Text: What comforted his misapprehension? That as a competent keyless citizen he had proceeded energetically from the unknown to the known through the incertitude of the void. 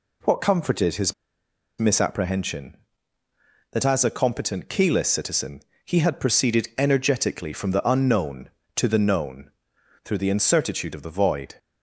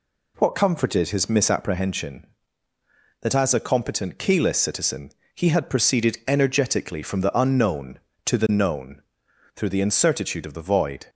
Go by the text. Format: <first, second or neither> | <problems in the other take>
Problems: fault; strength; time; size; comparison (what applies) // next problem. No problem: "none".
second | pauses between "his" and "misapprehension"; noticeable; at 1.1 s; 0.65 s long // pauses between "citizen" and "he"; slight; at 5.6 s; 0.22 s long; slight in the second // pauses between "known" and "through"; noticeable; at 9.5 s; 0.52 s long; noticeable in the second